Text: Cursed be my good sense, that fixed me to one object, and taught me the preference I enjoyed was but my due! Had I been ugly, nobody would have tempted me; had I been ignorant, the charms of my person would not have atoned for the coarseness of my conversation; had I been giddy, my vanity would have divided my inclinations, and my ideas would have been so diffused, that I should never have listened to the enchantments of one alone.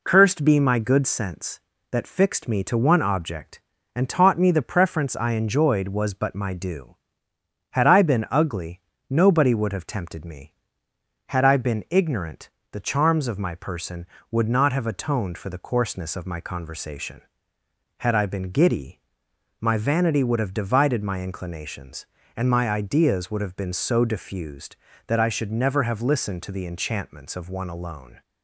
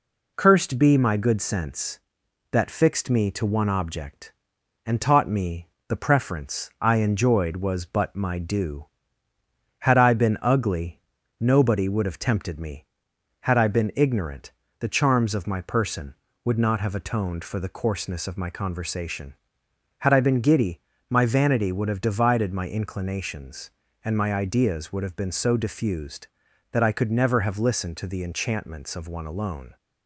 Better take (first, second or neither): first